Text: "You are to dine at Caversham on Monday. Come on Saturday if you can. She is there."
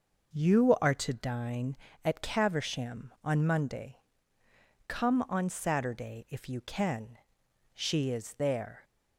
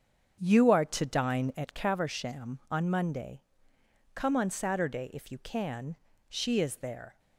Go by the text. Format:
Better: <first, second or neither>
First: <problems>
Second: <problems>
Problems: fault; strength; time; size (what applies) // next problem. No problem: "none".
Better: first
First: none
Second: starts louder than the rest; strong; until 1.9 s; 7.5 dB